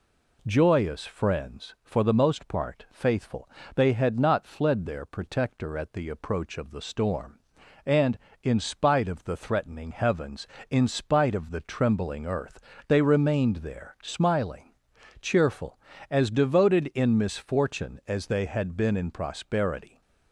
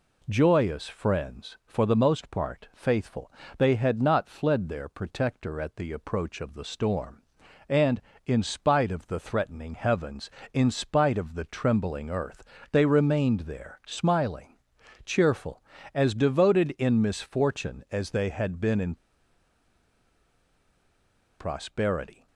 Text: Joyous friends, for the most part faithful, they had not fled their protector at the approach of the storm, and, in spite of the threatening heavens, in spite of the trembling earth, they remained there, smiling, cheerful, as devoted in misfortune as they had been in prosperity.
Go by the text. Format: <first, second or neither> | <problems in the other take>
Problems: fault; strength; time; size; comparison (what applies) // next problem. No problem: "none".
first | pauses between "in" and "prosperity"; strong; at 18.9 s; 2.4 s long